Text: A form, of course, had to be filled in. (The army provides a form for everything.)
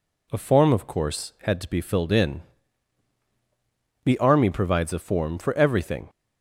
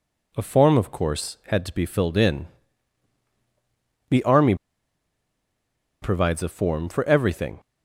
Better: first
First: none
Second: pauses between "army" and "provides"; strong; at 4.5 s; 1.4 s long

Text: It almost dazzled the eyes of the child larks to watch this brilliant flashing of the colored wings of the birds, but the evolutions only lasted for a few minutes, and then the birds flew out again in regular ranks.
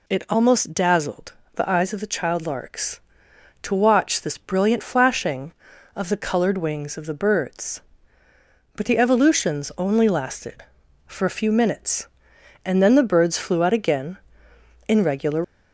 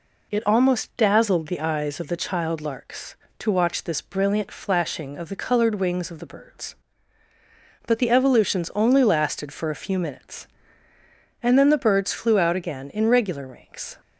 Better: second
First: pauses between "dazzled" and "the"; slight; at 1.3 s; 0.22 s long // stops before "ranks"; at 15.4 s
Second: none

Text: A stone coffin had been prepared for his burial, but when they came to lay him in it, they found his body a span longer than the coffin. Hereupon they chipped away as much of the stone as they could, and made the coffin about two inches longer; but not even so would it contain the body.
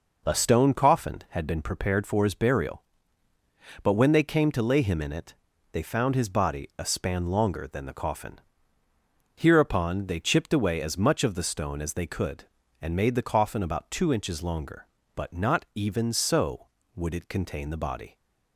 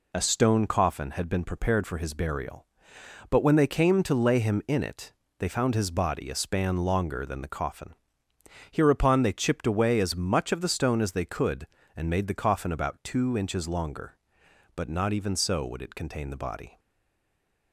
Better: first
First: none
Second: stays silent after the last word; from 16.7 s on; 1.0 s long

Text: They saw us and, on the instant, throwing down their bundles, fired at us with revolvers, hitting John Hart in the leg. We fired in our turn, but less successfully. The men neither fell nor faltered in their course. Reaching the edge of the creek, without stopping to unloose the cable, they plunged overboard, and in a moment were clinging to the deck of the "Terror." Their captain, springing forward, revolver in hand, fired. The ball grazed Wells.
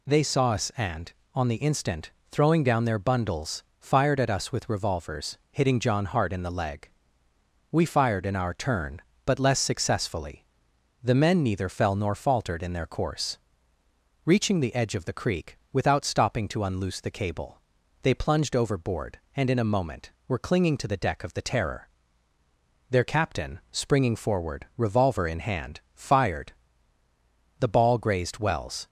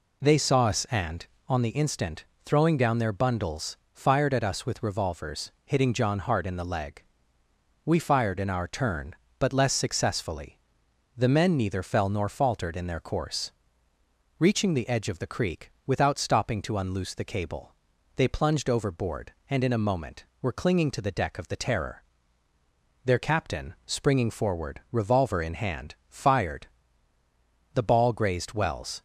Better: first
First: none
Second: starts louder than the rest; slight; until 1.7 s; 3 dB

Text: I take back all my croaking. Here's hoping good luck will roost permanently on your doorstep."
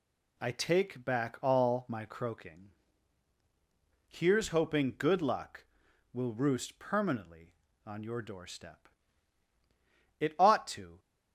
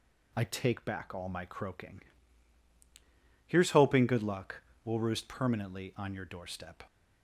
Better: second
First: goes on to say "It ought to"; noticeable; from 10.1 s on; 0.80 s long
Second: none

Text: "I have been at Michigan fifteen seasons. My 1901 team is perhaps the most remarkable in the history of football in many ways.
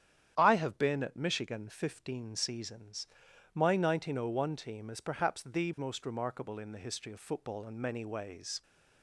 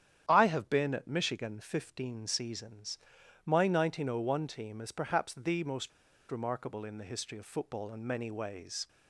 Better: first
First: starts louder than the rest; strong; until 1.3 s; 9.5 dB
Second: starts louder than the rest; strong; until 1.3 s; 9.5 dB // pauses between "most" and "remarkable"; at 5.9 s; 0.41 s long

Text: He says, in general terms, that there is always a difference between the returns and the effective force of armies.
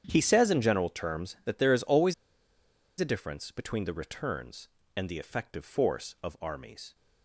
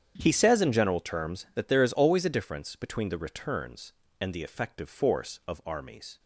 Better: second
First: starts louder than the rest; strong; until 1.0 s; 8.5 dB // pauses between "always" and "a"; noticeable; at 2.1 s; 0.84 s long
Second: starts louder than the rest; strong; until 1.1 s; 8.5 dB

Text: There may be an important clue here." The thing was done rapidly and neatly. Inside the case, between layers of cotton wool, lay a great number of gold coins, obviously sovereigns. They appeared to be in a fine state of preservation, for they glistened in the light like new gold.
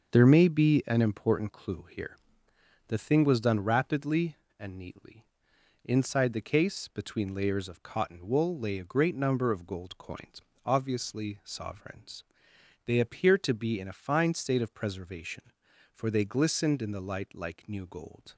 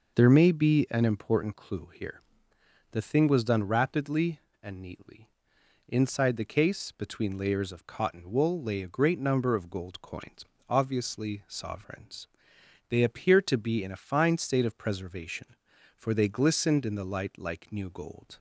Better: second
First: gets quieter; throughout; 6.5 dB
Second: none

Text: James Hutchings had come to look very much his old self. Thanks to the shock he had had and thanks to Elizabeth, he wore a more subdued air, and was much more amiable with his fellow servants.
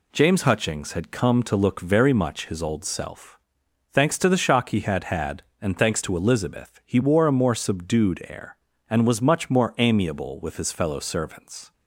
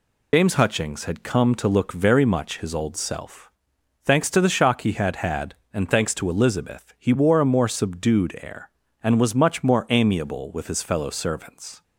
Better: first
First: none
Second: loses the start of "James"; at 0.3 s; 95 ms

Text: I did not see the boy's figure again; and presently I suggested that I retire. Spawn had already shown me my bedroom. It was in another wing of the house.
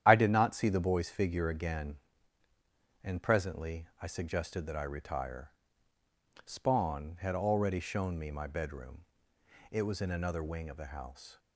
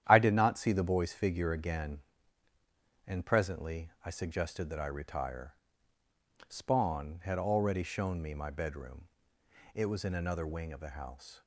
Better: second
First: loses the start of "I"; at 0.0 s; 30 ms // starts louder than the rest; strong; until 1.0 s; 10.5 dB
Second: starts louder than the rest; strong; until 1.0 s; 10.5 dB

